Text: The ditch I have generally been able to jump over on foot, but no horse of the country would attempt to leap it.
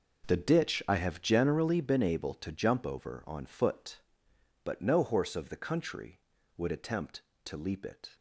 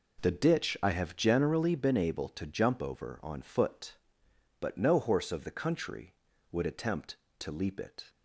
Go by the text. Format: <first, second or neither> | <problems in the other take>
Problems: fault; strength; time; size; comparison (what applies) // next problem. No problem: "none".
second | gets quieter; strong; throughout; 15.5 dB